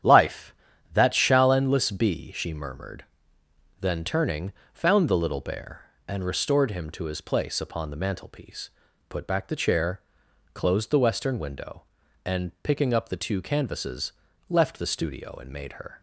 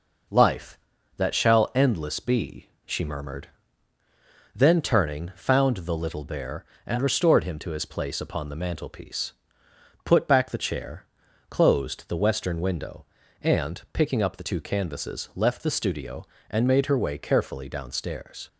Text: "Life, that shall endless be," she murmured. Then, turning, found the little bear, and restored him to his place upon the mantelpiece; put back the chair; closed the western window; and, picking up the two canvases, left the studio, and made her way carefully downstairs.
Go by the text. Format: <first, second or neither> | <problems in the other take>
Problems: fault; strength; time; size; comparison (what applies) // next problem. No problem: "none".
second | starts louder than the rest; strong; until 1.4 s; 10 dB // stops before "way carefully downstairs"; at 15.9 s